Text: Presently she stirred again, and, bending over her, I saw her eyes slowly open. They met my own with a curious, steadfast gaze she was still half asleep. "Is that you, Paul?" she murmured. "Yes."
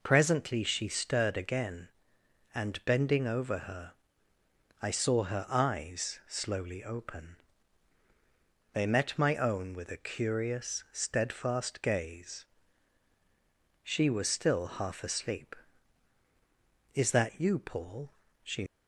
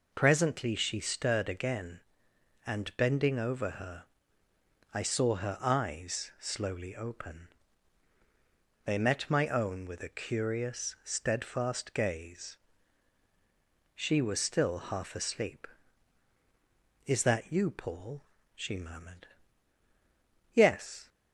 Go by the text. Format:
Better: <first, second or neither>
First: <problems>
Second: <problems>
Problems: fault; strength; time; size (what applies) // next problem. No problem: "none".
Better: second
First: pauses between "gaze" and "she"; strong; at 12.4 s; 1.3 s long // stops before "murmured Yes"; at 18.6 s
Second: pauses between "gaze" and "she"; strong; at 12.5 s; 1.3 s long